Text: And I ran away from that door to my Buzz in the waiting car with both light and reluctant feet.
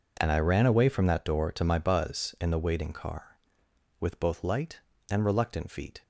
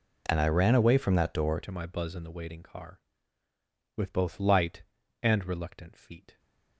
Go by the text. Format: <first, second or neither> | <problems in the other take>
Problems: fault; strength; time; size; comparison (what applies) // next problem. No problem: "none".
first | changes voice at "to"; from 1.6 s on; 4.7 s long